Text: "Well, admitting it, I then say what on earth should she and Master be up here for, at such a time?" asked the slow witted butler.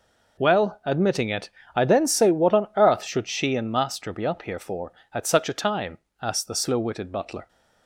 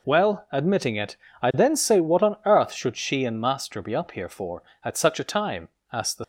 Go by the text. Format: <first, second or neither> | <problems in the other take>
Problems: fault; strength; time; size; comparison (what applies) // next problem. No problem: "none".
first | stops before "slow witted butler"; at 6.2 s